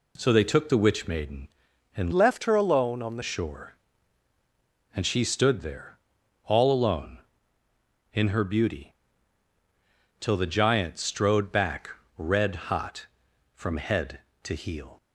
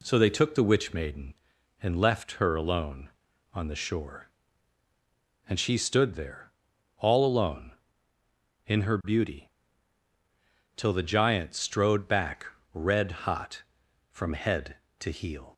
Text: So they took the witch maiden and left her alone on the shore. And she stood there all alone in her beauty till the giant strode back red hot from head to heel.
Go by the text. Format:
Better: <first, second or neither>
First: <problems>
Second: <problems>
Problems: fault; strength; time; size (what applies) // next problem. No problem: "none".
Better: second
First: changes voice from "left" to "the"; from 2.1 to 3.2 s; 1.1 s long // pauses between "there" and "all"; noticeable; at 5.9 s; 0.48 s long // pauses between "beauty" and "till"; strong; at 8.9 s; 1.2 s long // pauses between "back" and "red"; slight; at 11.8 s; 0.28 s long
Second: pauses between "there" and "all"; noticeable; at 6.5 s; 0.48 s long // pauses between "beauty" and "till"; strong; at 9.4 s; 1.2 s long // pauses between "back" and "red"; slight; at 12.4 s; 0.28 s long